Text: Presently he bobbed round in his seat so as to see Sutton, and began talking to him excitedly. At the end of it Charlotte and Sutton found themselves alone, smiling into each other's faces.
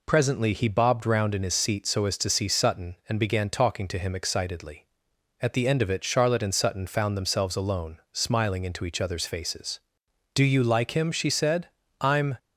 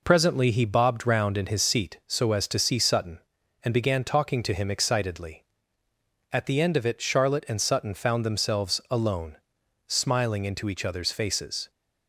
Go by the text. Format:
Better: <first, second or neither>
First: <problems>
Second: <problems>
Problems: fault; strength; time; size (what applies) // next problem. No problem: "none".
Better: second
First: goes on to say "Do you like him she said I'm"; strong; from 10.3 s on; 2.0 s long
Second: none